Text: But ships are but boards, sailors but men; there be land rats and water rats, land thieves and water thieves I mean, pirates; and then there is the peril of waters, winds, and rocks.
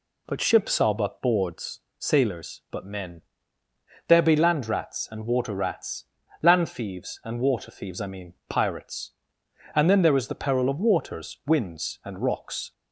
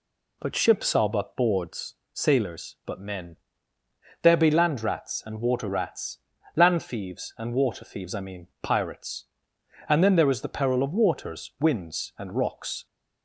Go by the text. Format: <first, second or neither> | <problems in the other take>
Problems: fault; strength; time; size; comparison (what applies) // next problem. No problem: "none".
neither | none